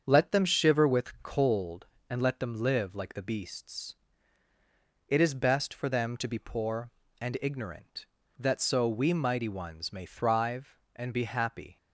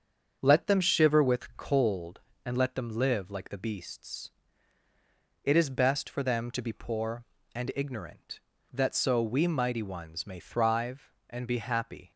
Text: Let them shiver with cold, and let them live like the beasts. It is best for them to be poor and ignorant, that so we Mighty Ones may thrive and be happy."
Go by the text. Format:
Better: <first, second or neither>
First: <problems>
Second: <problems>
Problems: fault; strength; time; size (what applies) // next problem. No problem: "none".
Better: neither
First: starts louder than the rest; strong; until 1.0 s; 7 dB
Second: starts louder than the rest; strong; until 1.4 s; 7 dB